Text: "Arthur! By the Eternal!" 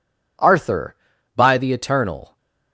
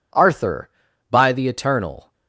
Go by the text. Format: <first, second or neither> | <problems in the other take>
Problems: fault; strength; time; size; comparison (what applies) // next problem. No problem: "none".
neither | none